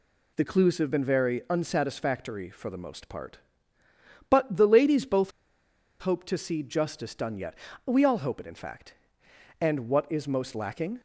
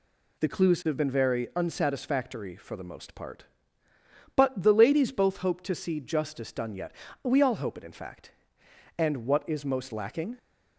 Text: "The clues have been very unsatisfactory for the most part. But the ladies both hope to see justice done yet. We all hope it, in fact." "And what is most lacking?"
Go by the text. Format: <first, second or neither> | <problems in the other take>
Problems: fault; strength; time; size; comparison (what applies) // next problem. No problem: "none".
second | pauses between "both" and "hope"; noticeable; at 5.3 s; 0.69 s long